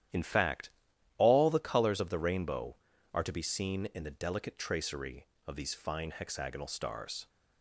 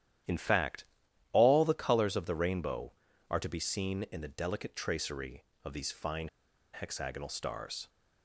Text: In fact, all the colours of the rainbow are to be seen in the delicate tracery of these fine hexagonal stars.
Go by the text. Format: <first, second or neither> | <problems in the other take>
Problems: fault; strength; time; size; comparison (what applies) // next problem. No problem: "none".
first | starts louder than the rest; strong; until 1.7 s; 11.5 dB; strong in the first // pauses between "fine" and "hexagonal"; at 6.2 s; 0.44 s long